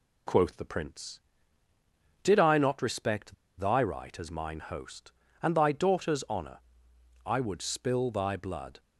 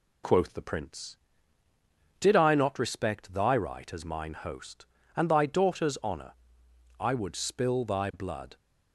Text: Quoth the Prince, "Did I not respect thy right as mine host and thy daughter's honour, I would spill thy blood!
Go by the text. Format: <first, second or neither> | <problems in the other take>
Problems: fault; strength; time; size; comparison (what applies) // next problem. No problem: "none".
second | pauses between "respect" and "thy"; slight; at 3.3 s; 0.25 s long